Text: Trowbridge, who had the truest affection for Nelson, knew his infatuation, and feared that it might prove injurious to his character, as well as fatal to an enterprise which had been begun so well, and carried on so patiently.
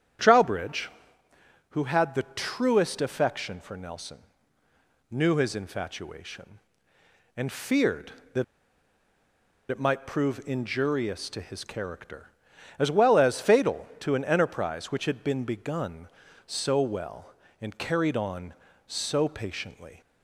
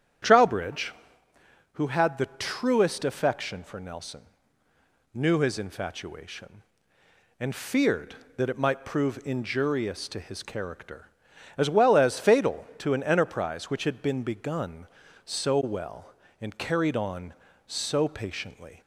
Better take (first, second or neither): second